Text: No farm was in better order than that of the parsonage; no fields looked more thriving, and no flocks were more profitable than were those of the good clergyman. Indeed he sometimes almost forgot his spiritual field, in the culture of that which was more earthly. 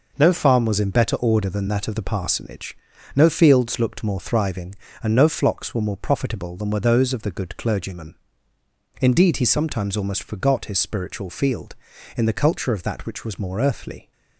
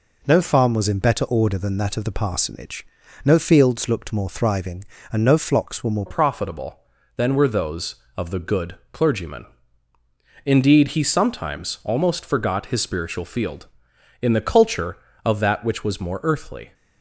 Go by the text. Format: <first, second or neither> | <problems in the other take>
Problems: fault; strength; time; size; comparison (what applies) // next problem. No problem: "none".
first | changes voice at "profitable"; from 6.0 s on; 10.7 s long